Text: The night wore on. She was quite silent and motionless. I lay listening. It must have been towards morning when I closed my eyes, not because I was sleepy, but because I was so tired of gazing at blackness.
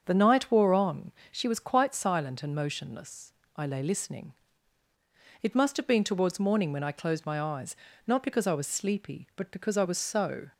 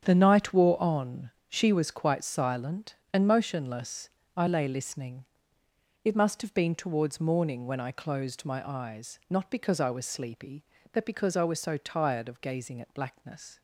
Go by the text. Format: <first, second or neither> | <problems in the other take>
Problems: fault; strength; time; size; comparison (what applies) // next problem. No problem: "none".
second | starts louder than the rest; until 1.0 s; 7 dB; strong in the second // stops before "tired of gazing at blackness"; at 10.5 s